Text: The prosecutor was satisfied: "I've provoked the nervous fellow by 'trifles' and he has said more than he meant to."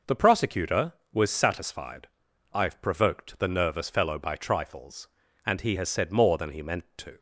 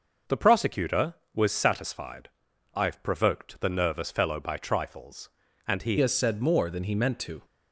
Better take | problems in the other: first | changes voice at "has"; from 5.9 s on; 1.5 s long

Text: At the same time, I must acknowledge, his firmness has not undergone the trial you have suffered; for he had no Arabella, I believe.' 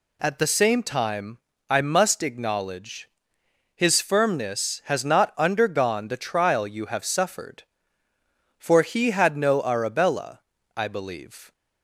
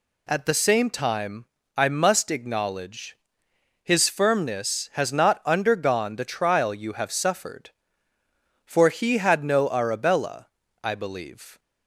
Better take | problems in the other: neither | none

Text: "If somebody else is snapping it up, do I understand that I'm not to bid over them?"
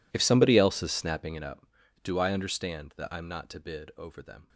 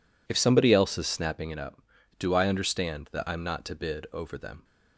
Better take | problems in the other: second | gets quieter; strong; throughout; 23.5 dB

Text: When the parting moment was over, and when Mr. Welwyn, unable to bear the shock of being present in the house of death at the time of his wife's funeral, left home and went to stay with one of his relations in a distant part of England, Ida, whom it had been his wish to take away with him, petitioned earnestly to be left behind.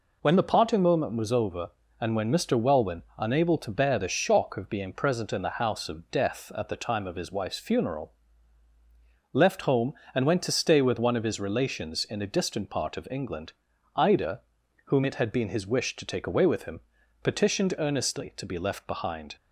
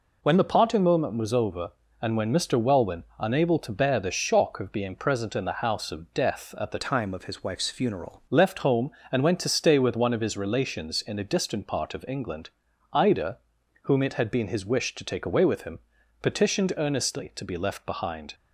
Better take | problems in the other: first | changes voice from "time" to "funeral"; from 6.7 to 8.2 s; 1.5 s long

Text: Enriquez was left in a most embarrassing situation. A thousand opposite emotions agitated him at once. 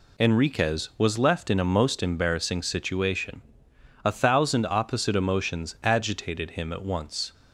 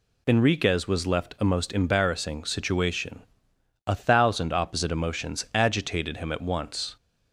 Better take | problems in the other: first | skips "in"; at 1.3 s

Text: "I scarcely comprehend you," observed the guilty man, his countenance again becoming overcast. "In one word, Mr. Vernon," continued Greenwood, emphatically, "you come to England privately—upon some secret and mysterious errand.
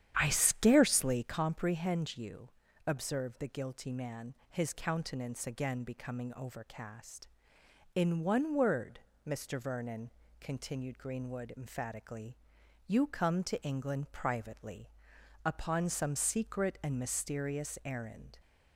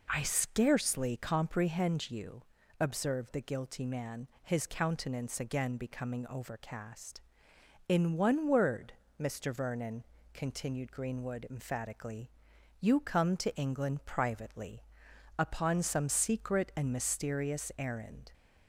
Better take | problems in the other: second | starts louder than the rest; strong; until 1.4 s; 10 dB

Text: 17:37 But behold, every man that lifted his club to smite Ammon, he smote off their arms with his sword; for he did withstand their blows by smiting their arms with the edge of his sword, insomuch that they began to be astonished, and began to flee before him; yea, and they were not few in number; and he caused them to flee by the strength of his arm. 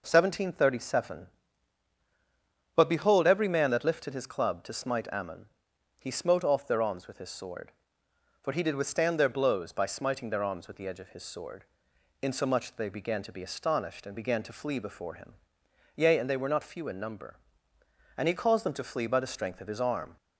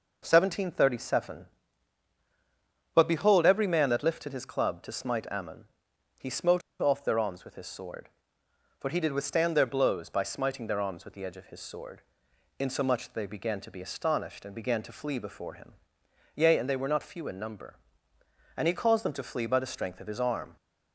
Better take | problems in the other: first | pauses between "smote" and "off"; slight; at 6.6 s; 0.20 s long

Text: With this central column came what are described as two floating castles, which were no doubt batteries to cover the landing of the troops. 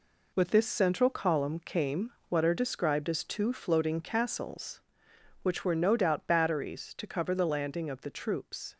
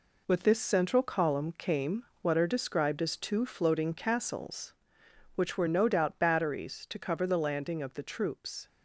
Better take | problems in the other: neither | pauses between "came" and "what"; slight; the same in both

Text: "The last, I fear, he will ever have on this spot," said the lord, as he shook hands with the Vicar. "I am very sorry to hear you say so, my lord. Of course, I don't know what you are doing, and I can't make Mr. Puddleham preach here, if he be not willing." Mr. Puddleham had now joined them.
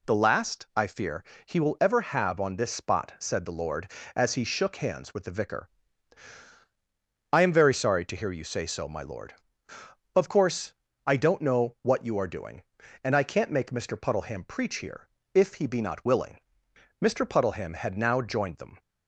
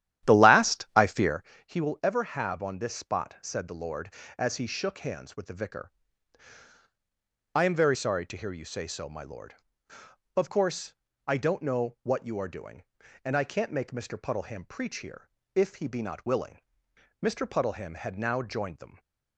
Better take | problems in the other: first | starts louder than the rest; strong; until 1.4 s; 11.5 dB

